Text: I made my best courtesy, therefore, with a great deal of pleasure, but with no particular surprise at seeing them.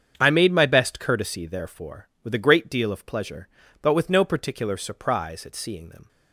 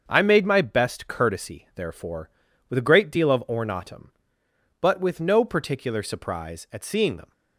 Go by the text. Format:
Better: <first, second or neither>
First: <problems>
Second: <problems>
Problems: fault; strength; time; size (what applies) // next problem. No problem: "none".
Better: first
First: starts louder than the rest; strong; until 1.1 s; 7.5 dB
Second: starts louder than the rest; until 1.0 s; 6.5 dB // says "ornatum" for "pleasure"; at 3.4 s